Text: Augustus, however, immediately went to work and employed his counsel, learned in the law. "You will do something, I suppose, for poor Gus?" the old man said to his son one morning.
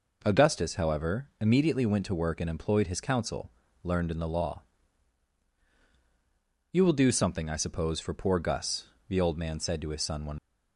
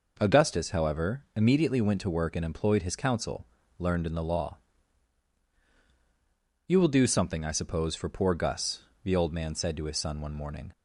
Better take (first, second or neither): second